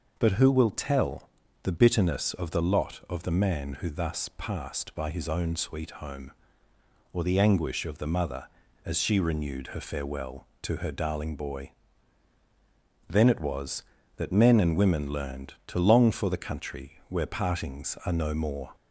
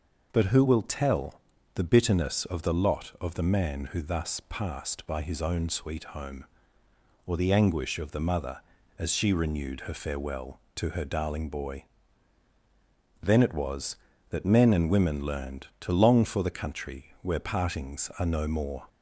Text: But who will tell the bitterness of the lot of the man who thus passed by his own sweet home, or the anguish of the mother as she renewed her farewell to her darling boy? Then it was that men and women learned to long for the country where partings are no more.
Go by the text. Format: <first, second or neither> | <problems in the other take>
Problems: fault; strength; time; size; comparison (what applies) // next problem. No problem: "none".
neither | pauses between "tell" and "the"; slight; the same in both